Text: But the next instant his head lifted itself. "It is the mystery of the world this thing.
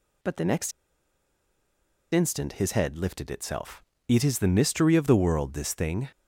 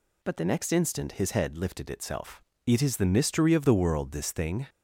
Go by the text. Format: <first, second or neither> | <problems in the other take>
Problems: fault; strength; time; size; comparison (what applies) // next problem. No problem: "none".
second | pauses between "next" and "instant"; strong; at 0.7 s; 1.4 s long